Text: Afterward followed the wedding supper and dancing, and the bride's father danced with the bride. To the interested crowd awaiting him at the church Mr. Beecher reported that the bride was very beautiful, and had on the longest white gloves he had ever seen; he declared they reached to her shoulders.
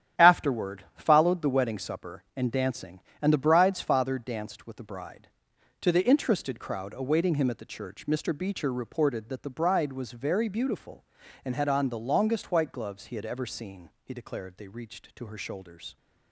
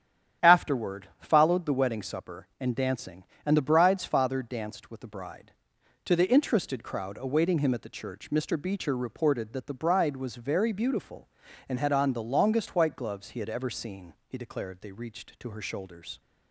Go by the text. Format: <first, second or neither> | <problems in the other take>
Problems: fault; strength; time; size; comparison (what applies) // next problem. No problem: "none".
second | gets quieter; strong; throughout; 9 dB // starts louder than the rest; strong; until 1.3 s; 10.5 dB; strong in the second